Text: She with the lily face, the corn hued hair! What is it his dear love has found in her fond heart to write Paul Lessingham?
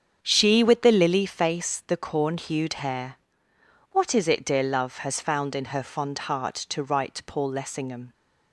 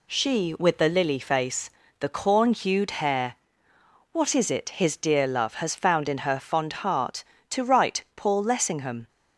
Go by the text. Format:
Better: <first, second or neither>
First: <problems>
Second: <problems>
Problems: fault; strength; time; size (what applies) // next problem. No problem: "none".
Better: second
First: starts louder than the rest; strong; until 1.2 s; 7.5 dB // skips "his"; at 4.4 s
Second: none